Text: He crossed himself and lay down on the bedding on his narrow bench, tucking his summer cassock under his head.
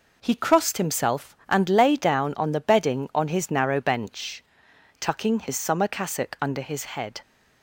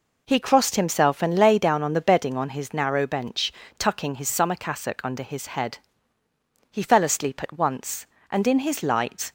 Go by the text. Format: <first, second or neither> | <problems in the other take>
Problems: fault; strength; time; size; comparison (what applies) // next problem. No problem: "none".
first | goes on to say "He fell asleep at once and in his light"; strong; from 6.7 s on; 2.6 s long